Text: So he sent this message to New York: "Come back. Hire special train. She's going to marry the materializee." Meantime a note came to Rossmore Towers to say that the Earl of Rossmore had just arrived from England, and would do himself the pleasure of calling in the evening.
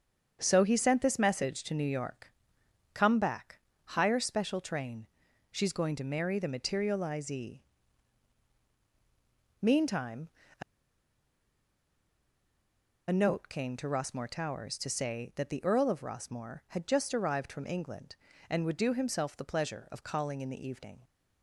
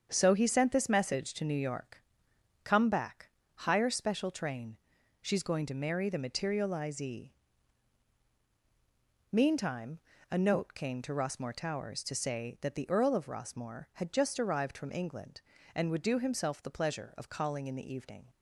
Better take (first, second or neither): second